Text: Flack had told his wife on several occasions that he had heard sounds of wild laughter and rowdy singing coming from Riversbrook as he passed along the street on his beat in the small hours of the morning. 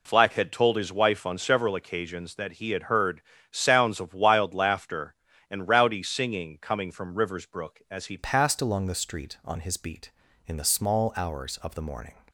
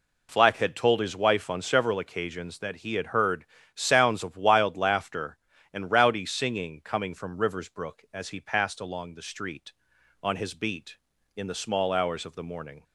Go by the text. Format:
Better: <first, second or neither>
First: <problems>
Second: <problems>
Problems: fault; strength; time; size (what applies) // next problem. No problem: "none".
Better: second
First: pauses between "heard" and "sounds"; slight; at 3.2 s; 0.28 s long // changes voice at "passed"; from 8.1 s on; 4.0 s long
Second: pauses between "heard" and "sounds"; slight; at 3.4 s; 0.28 s long